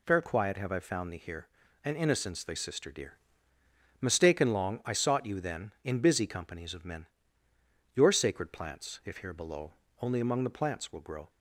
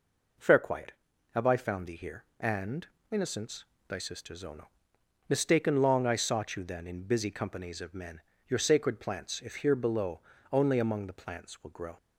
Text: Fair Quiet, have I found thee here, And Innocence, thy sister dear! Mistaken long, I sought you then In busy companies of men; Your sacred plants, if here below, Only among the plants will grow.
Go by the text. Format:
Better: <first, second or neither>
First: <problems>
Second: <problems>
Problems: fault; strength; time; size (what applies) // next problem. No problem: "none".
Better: first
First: none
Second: pauses between "And" and "Innocence"; slight; at 2.8 s; 0.24 s long // says "zono" for "dear"; at 4.3 s